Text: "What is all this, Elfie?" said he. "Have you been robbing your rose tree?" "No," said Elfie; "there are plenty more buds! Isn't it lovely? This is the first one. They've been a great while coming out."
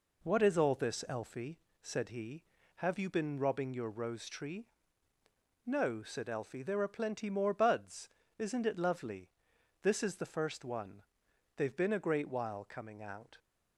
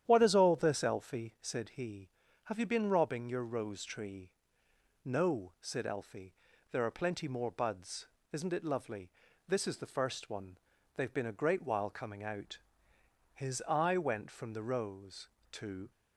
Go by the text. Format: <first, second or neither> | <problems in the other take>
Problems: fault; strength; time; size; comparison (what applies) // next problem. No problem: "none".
first | starts louder than the rest; strong; until 1.0 s; 10 dB // goes on to say "His eye went from the rose to"; strong; from 13.3 s on; 2.5 s long